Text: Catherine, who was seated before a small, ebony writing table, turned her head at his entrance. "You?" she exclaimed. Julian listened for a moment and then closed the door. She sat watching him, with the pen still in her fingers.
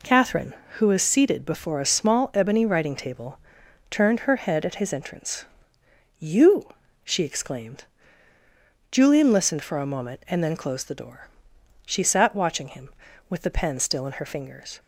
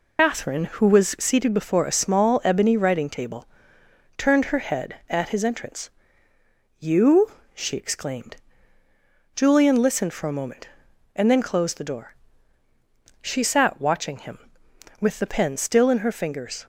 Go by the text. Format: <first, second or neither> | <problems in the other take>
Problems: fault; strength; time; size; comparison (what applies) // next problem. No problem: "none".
first | loses the start of "Catherine"; at 0.1 s; 115 ms